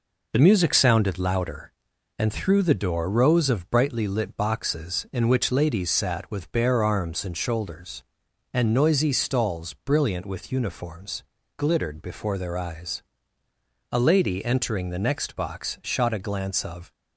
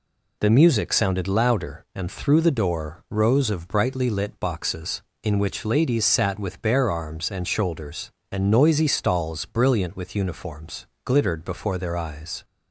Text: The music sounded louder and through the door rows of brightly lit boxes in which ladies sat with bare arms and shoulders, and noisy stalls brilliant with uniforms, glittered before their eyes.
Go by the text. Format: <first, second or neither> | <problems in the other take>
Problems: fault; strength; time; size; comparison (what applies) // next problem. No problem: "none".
second | goes on to say "A lady entering the next box shot a glance of"; strong; from 13.9 s on; 3.0 s long